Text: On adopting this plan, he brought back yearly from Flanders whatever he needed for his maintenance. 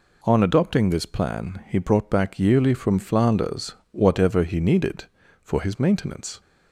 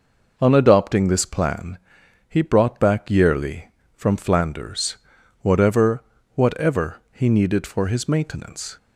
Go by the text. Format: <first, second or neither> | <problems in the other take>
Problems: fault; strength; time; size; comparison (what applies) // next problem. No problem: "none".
first | pauses between "Flanders" and "whatever"; at 4.9 s; 0.44 s long; slight in the first // says "whatever" twice; at 6.3 s